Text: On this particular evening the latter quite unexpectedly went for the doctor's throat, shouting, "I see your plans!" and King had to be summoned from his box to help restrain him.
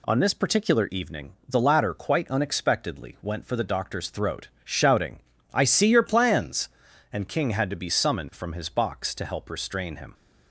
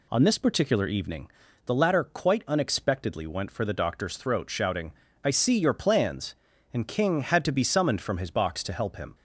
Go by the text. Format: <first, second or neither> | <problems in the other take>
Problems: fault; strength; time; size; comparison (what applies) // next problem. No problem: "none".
first | pauses between "evening" and "the"; at 1.2 s; 0.38 s long; slight in the first // skips "restrain"; at 8.9 s